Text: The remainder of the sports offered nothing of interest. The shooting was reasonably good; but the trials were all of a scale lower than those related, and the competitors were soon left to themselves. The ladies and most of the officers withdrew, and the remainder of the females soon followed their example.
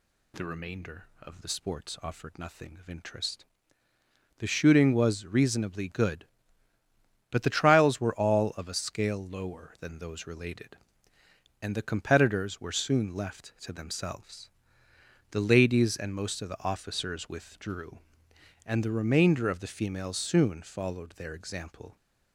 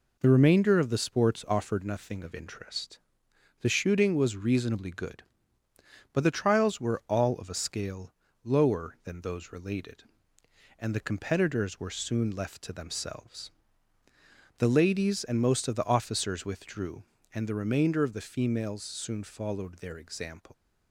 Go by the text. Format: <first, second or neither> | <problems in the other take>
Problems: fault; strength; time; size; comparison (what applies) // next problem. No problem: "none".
first | pauses between "scale" and "lower"; slight; at 8.1 s; 0.28 s long // leaves "example" unfinished; at 20.5 s; 95 ms